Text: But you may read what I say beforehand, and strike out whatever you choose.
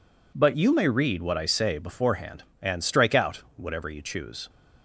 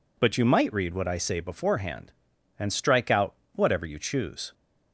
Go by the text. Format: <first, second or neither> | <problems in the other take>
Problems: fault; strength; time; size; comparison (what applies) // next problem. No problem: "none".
first | says "might" for "may"; at 0.4 s // pauses between "out" and "whatever"; slight; at 3.3 s; 0.20 s long